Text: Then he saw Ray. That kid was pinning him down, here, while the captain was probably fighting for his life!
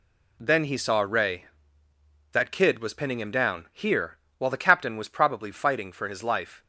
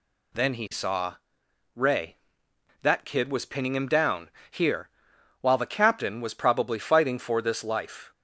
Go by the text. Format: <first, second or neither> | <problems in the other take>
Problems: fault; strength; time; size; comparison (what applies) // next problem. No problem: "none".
first | pauses between "saw" and "Ray"; noticeable; at 1.1 s; 0.58 s long // says "this" for "his"; at 7.4 s